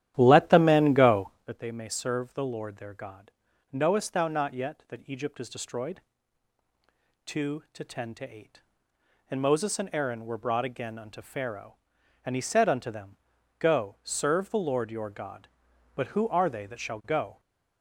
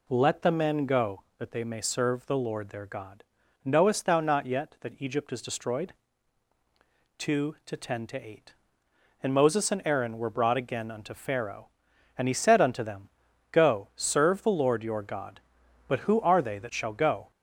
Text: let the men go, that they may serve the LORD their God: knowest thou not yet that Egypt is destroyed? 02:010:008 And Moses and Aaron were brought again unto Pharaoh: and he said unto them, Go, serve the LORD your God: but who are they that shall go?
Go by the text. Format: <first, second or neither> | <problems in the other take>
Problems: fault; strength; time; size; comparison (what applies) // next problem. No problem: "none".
second | starts louder than the rest; strong; until 1.5 s; 12 dB